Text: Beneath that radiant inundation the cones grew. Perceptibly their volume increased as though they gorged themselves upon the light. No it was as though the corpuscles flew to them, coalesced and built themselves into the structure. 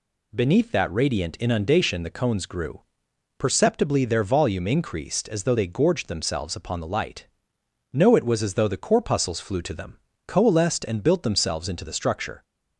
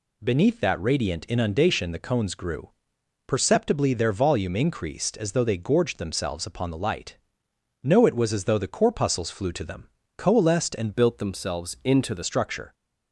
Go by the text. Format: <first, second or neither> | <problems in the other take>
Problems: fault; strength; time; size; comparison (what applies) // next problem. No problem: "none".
first | changes voice from "built" to "the"; from 10.9 to 12.2 s; 1.3 s long